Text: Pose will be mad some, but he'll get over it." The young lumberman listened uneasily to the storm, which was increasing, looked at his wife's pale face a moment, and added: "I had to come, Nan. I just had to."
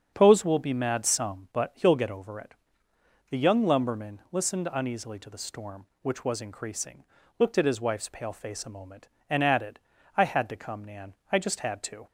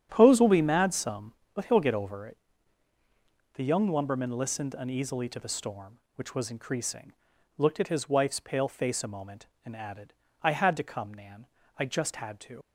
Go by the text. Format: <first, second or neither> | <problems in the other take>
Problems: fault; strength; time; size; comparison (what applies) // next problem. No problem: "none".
first | starts louder than the rest; strong; until 1.1 s; 9.5 dB; strong in the first // leaves "to" unfinished; at 12.6 s; 80 ms